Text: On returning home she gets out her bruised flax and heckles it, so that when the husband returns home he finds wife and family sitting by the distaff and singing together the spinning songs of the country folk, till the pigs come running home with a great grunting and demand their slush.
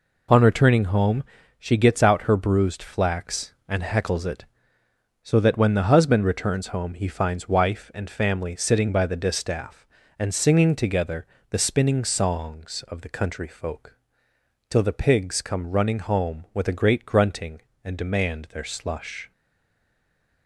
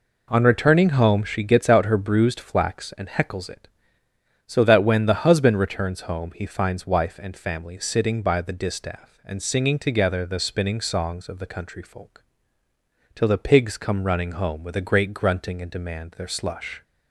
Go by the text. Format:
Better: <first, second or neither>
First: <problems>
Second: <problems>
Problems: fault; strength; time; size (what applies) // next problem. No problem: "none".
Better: second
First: pauses between "home" and "she"; slight; at 1.2 s; 0.34 s long // pauses between "together" and "the"; slight; at 11.2 s; 0.24 s long // stays silent after the last word; noticeable; from 19.3 s on; 1.1 s long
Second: none